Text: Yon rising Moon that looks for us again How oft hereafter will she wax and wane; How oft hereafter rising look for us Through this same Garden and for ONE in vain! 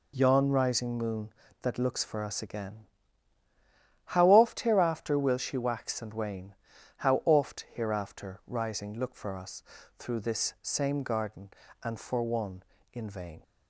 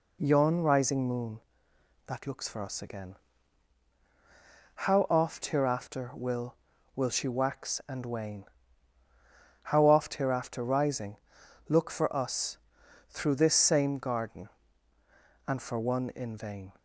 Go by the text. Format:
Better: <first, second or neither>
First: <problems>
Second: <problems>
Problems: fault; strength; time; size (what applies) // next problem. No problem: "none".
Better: first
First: pauses between "again" and "How"; at 2.8 s; 1.2 s long // pauses between "us" and "Through"; slight; at 9.6 s; 0.34 s long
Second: pauses between "again" and "How"; strong; at 3.1 s; 1.6 s long // says "will" twice; at 6.9 s // pauses between "rising" and "look"; noticeable; at 11.1 s; 0.54 s long // pauses between "us" and "Through"; noticeable; at 12.5 s; 0.52 s long